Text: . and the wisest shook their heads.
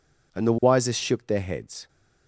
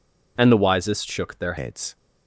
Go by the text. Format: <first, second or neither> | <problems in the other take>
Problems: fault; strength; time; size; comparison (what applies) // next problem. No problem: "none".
first | changes voice from "and" to "their"; from 0.3 to 1.5 s; 1.2 s long